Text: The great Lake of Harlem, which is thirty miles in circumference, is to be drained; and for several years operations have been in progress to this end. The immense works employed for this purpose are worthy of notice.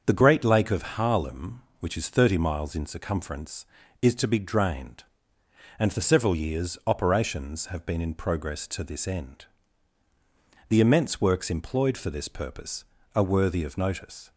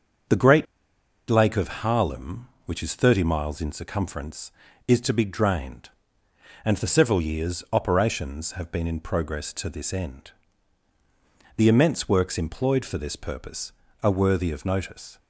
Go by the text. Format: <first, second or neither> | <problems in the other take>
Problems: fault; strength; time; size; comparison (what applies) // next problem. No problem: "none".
first | starts louder than the rest; until 1.9 s; 7 dB; also in the first // pauses between "great" and "Lake"; noticeable; at 0.6 s; 0.65 s long